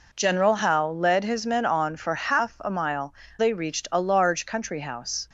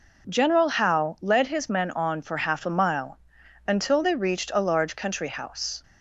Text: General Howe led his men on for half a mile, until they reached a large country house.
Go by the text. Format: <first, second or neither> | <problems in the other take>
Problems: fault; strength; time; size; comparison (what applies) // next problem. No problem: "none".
second | skips "until"; at 3.2 s